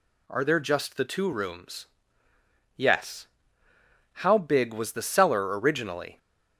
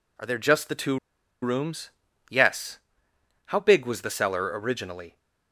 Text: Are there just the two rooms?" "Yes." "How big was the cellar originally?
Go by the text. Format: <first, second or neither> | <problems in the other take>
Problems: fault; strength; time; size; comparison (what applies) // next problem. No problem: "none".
first | pauses between "two" and "rooms"; at 0.9 s; 0.45 s long